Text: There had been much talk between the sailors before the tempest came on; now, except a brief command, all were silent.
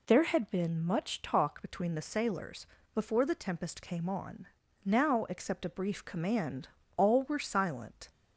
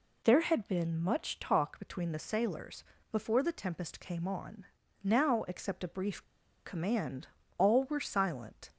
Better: first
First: pauses between "sailors" and "before"; slight; at 2.6 s; 0.26 s long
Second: pauses between "sailors" and "before"; slight; at 2.8 s; 0.26 s long // pauses between "brief" and "command"; at 6.2 s; 0.42 s long

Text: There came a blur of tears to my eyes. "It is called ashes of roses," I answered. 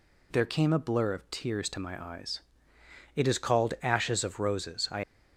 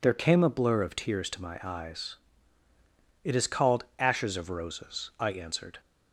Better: second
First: stops before "answered"; at 5.0 s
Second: none

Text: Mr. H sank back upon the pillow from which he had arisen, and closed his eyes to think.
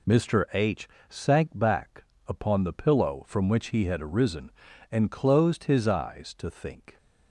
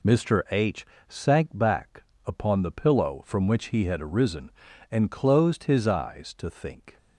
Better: neither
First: pauses between "H" and "sank"; slight; at 0.8 s; 0.22 s long // pauses between "back" and "upon"; slight; at 2.0 s; 0.22 s long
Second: pauses between "H" and "sank"; slight; at 0.8 s; 0.24 s long // pauses between "back" and "upon"; slight; at 2.0 s; 0.21 s long

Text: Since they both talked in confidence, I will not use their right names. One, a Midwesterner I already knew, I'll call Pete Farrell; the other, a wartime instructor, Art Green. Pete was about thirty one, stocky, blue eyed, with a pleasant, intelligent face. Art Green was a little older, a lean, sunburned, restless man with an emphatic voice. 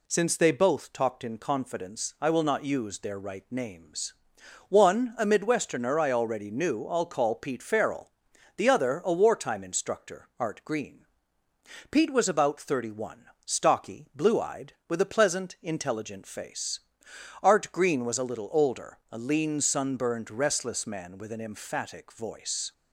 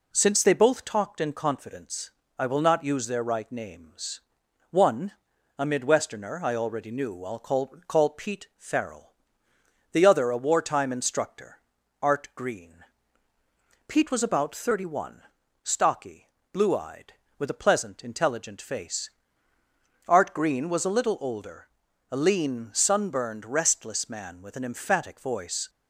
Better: first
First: none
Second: says "call" twice; at 7.8 s

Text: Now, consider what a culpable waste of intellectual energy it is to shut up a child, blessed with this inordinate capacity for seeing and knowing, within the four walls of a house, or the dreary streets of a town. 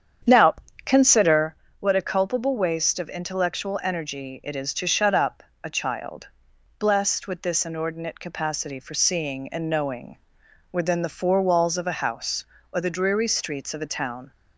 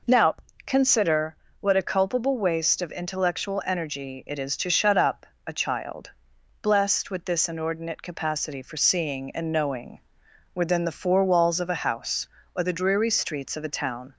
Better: second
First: starts louder than the rest; strong; until 1.6 s; 8.5 dB // pauses between "consider" and "what"; slight; at 1.5 s; 0.28 s long // pauses between "up" and "a"; slight; at 5.4 s; 0.20 s long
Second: pauses between "consider" and "what"; slight; at 1.3 s; 0.28 s long // pauses between "up" and "a"; slight; at 5.2 s; 0.20 s long

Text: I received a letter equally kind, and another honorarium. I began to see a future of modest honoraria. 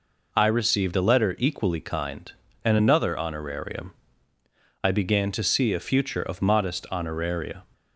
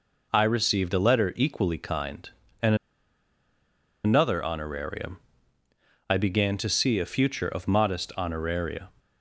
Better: first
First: none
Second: pauses between "and" and "another"; strong; at 2.7 s; 1.2 s long

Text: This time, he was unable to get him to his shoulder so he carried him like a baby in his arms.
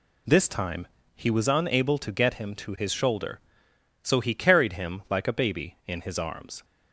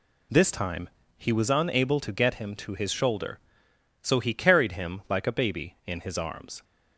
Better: neither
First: none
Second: none

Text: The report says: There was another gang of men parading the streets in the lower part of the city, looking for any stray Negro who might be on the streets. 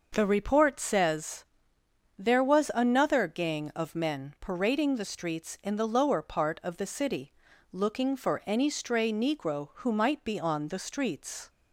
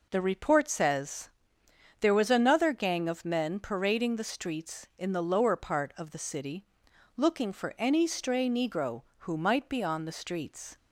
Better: neither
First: none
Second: none

